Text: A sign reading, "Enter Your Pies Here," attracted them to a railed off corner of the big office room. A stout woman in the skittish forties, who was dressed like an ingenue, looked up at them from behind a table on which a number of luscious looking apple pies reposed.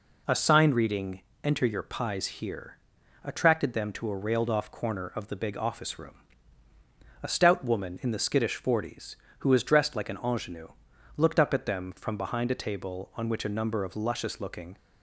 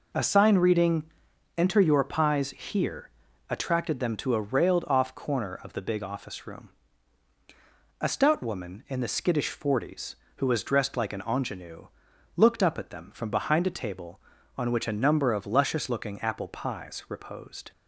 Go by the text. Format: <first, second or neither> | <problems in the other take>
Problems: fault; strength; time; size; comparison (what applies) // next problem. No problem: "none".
second | stops before "apple pies reposed"; at 14.7 s